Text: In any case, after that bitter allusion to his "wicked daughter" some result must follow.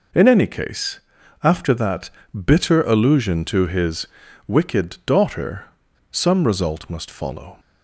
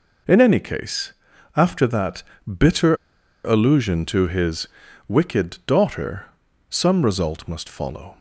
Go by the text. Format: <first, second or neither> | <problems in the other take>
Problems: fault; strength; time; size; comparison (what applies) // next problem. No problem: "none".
first | pauses between "that" and "bitter"; slight; at 2.2 s; 0.24 s long; slight in the first // pauses between "bitter" and "allusion"; noticeable; at 2.9 s; 0.50 s long // pauses between "his" and "wicked"; at 4.6 s; 0.40 s long; also in the first // pauses between "daughter" and "some"; at 6.2 s; 0.44 s long; noticeable in the first